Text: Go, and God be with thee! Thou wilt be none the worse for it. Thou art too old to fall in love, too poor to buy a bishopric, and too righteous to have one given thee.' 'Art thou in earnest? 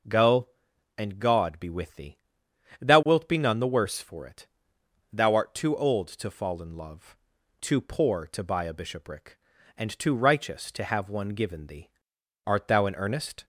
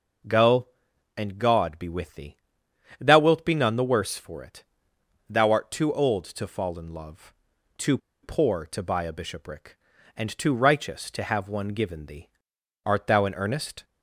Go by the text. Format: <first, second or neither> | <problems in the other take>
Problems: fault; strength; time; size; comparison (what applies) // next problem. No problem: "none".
first | pauses between "too" and "poor"; slight; at 7.9 s; 0.25 s long